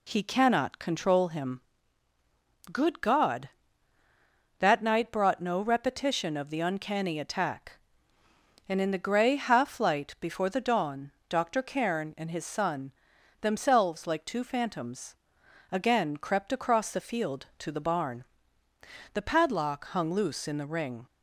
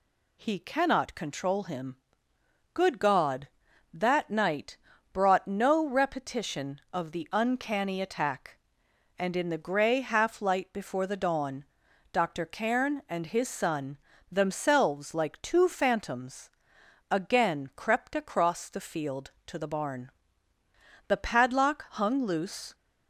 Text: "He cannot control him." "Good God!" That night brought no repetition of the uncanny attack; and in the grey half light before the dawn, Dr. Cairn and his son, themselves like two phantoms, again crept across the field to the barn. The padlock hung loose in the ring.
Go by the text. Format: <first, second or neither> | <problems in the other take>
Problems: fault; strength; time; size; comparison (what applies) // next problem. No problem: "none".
first | pauses between "night" and "brought"; slight; at 4.7 s; 0.36 s long // stops before "in the ring"; at 22.7 s